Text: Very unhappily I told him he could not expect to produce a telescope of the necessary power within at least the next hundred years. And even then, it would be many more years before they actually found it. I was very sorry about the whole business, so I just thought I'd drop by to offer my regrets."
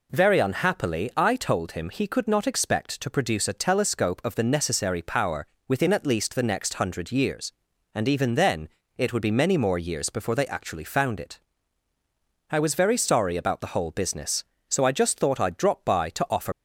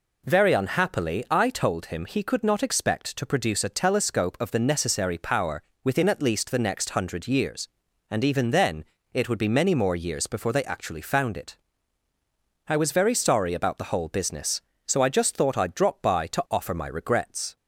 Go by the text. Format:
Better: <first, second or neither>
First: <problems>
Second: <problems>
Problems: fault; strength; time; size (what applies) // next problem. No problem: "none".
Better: second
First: pauses between "power" and "within"; slight; at 5.4 s; 0.20 s long // stops before "my regrets"; at 16.5 s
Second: pauses between "power" and "within"; slight; at 5.6 s; 0.20 s long